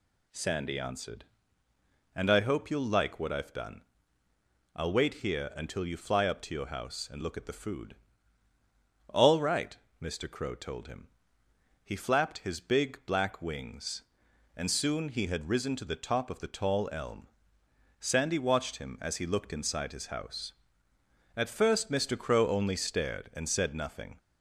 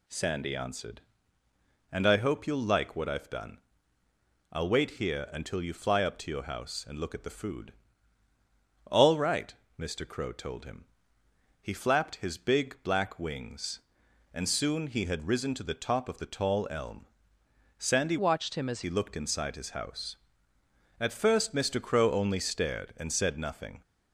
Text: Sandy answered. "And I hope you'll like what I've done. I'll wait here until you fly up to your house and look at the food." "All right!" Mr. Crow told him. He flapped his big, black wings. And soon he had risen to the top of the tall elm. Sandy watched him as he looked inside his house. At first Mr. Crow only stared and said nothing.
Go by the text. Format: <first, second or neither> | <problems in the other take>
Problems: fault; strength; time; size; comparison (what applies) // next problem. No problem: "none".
first | changes voice from "watched" to "as"; from 18.1 to 18.8 s; 0.7 s long